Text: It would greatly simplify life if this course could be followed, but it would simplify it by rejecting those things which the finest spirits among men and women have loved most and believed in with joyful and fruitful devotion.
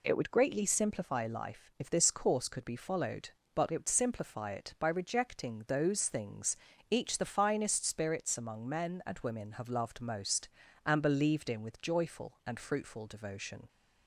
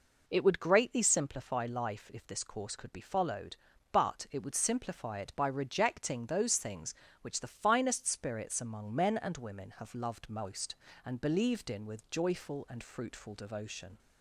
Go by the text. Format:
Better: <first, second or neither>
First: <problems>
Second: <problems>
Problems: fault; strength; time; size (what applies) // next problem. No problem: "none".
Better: second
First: says "each" for "which"; at 6.9 s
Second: none